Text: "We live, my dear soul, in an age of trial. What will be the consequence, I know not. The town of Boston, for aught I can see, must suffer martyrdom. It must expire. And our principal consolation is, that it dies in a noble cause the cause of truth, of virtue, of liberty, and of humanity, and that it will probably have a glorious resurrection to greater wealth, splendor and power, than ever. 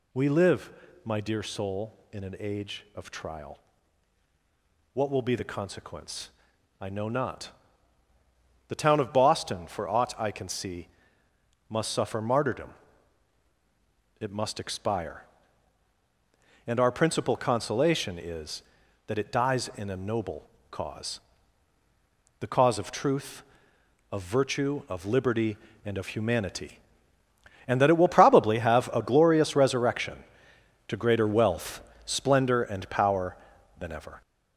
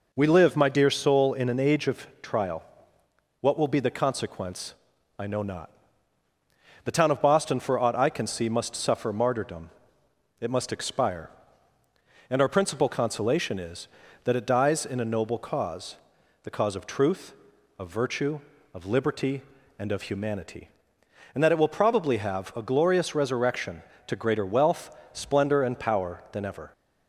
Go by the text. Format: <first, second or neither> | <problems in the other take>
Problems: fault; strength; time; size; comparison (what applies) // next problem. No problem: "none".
second | gets louder; throughout; 6.5 dB // pauses between "noble" and "cause"; slight; at 20.4 s; 0.22 s long // pauses between "cause" and "the"; at 21.1 s; 1.2 s long; noticeable in the second